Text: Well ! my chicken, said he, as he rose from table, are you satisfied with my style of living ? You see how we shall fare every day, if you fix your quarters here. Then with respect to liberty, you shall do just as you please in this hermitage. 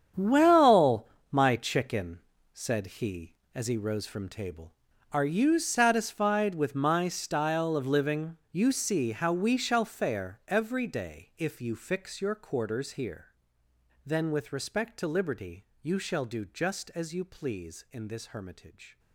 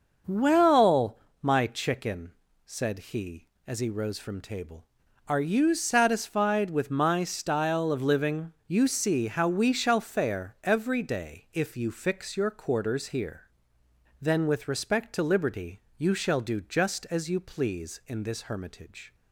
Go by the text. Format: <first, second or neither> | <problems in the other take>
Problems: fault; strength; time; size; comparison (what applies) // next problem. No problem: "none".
second | gets quieter; strong; throughout; 14.5 dB // starts louder than the rest; strong; until 1.4 s; 8 dB; noticeable in the second